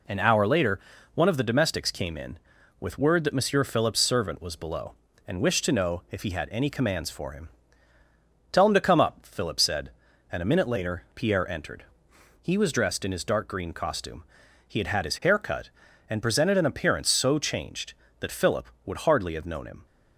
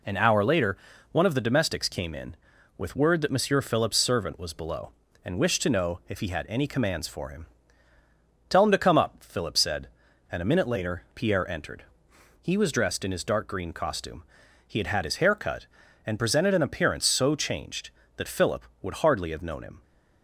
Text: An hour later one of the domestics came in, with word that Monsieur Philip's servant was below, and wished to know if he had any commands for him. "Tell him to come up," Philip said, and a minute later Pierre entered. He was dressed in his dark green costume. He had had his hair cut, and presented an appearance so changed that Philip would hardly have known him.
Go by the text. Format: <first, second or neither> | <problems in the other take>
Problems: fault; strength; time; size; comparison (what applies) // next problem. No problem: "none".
neither | pauses between "later" and "one"; slight; the same in both